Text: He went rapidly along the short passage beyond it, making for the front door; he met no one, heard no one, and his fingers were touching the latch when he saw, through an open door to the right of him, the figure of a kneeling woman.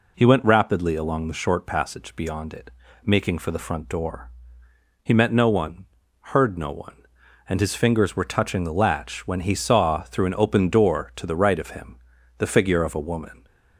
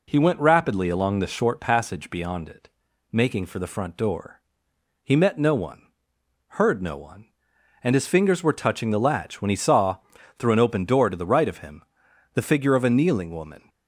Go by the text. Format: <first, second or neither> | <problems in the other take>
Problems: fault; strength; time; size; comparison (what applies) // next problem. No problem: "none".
second | skips "kneeling"; at 12.9 s